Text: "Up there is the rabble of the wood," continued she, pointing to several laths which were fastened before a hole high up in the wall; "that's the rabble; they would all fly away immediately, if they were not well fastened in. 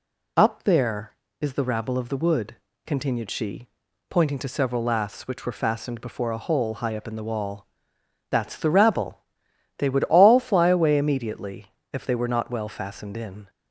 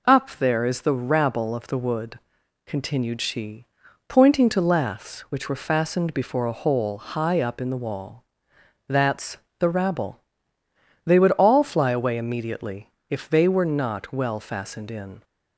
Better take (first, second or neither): first